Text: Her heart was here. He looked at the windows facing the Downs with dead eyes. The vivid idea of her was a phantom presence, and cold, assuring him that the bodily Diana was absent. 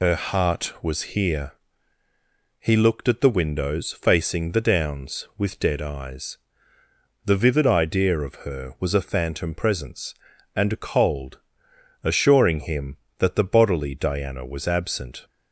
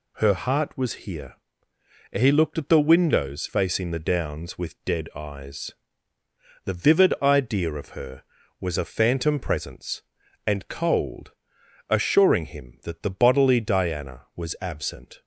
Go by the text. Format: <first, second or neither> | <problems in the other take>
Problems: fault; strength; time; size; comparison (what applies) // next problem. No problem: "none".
second | loses the start of "Her"; at 0.0 s; 80 ms